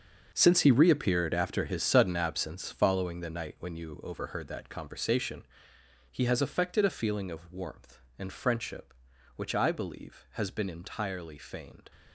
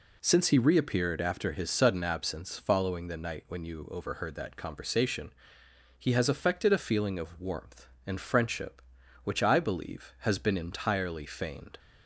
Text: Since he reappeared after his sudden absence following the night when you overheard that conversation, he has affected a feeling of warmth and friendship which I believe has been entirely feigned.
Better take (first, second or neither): second